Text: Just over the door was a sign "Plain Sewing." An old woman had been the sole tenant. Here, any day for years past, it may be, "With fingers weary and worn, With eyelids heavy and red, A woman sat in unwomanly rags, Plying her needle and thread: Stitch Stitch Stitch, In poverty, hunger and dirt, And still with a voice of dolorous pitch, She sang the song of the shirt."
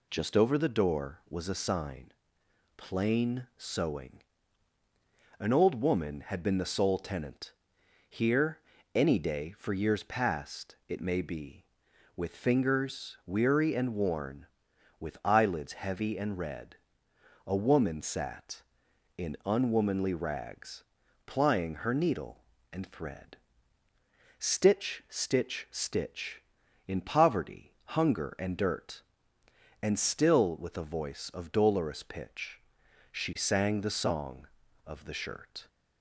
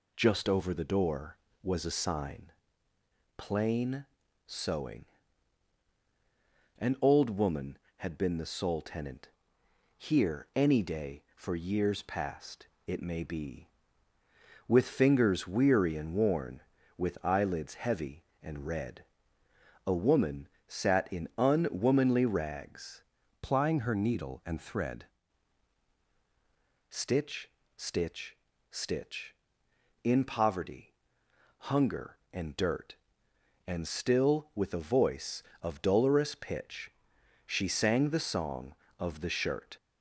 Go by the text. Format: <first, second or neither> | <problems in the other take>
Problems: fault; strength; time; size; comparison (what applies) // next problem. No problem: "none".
first | pauses between "sign" and "Plain"; noticeable; at 2.5 s; 0.84 s long; noticeable in the first // pauses between "Plain" and "Sewing"; at 4.0 s; 0.40 s long // pauses between "woman" and "sat"; slight; at 20.4 s; 0.20 s long // changes voice from "Plying" to "thread"; from 23.4 to 25.0 s; 1.6 s long // pauses between "Stitch" and "Stitch"; slight; at 27.5 s; 0.26 s long // pauses between "Stitch" and "Stitch"; slight; at 28.3 s; 0.34 s long